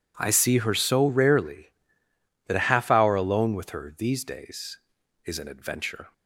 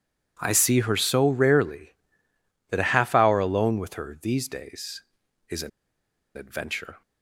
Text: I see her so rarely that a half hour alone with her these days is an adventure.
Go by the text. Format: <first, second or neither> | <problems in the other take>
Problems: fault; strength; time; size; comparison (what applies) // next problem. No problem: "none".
first | pauses between "an" and "adventure"; noticeable; at 5.7 s; 0.67 s long